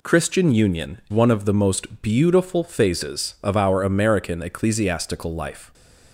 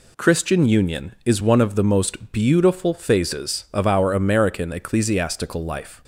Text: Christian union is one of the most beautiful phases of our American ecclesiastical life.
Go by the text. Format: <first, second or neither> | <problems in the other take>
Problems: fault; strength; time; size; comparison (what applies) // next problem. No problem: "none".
second | skips "is"; at 1.0 s // stays silent after the last word; slight; from 5.6 s on; 0.5 s long